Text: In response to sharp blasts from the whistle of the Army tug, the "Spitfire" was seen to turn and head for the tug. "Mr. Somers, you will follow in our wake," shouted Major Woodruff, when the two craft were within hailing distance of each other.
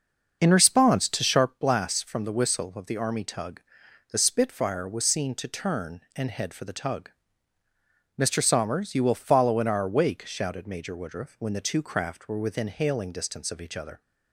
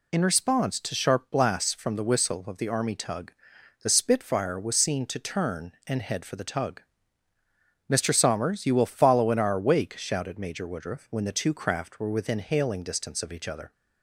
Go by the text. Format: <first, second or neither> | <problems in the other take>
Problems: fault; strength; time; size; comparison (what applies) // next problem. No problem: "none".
second | starts louder than the rest; until 1.4 s; 6 dB